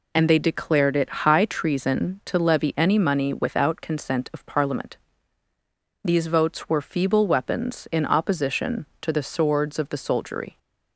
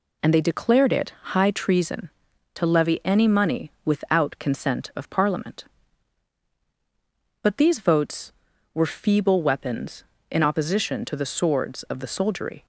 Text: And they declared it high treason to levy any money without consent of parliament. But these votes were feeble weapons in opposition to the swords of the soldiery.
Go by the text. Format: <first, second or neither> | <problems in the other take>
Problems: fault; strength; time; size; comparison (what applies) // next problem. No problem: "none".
second | skips "But"; at 5.4 s